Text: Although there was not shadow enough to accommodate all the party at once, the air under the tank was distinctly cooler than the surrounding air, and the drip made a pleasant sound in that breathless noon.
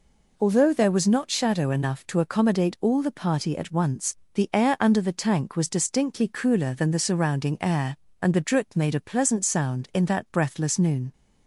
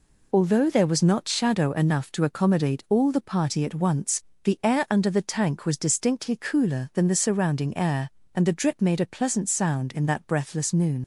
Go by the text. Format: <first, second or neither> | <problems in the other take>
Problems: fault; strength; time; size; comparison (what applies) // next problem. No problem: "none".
first | leaves "noon" unfinished; at 11.0 s; 75 ms